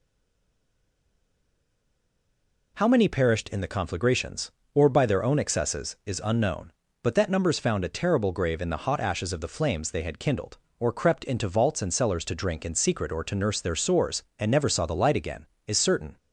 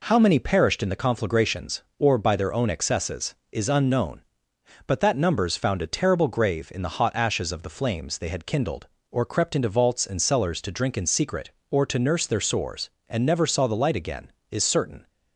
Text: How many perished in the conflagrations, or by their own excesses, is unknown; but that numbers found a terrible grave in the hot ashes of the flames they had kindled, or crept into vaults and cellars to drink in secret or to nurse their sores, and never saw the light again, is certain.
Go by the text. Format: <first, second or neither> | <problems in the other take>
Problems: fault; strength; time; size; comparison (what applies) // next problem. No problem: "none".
second | stays silent before the first word; strong; until 2.7 s; 2.7 s long